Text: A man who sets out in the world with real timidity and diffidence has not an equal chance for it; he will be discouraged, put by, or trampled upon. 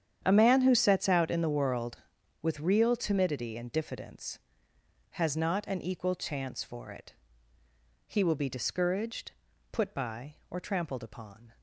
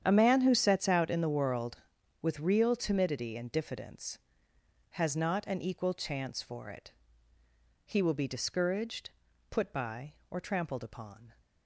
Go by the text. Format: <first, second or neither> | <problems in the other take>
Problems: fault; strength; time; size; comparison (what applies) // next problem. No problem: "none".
neither | starts louder than the rest; strong; the same in both